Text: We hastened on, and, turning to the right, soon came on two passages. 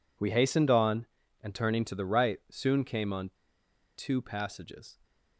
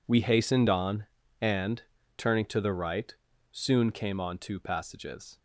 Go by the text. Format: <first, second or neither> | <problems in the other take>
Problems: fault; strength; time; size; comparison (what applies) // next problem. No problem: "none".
second | pauses between "on" and "two"; noticeable; at 3.2 s; 0.67 s long